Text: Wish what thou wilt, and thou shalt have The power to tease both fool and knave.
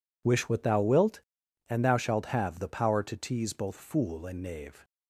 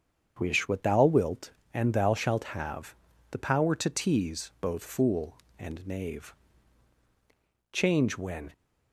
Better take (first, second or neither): first